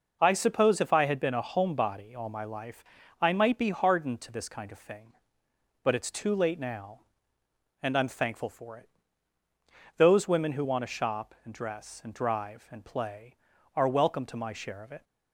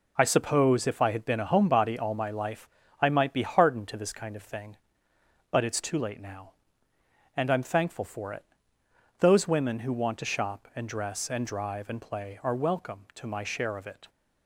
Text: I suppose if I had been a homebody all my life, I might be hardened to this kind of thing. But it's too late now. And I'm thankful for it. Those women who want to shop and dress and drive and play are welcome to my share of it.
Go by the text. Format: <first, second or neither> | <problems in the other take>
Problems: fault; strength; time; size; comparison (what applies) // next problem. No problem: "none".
neither | none